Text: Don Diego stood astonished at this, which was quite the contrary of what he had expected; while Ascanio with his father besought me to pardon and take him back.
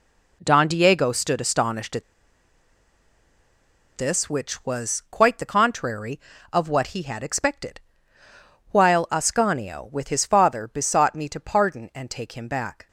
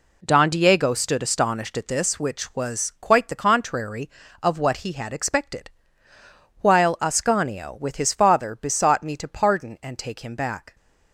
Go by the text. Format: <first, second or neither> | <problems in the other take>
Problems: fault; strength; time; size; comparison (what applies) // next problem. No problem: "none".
second | pauses between "at" and "this"; strong; at 2.0 s; 1.9 s long